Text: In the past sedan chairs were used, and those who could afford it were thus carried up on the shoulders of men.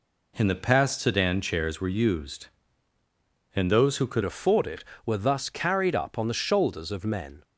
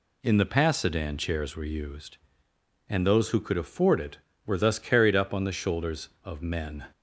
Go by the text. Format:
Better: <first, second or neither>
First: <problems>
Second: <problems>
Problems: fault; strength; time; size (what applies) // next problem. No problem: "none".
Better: second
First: changes voice at "afford"; from 4.2 s on; 3.2 s long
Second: none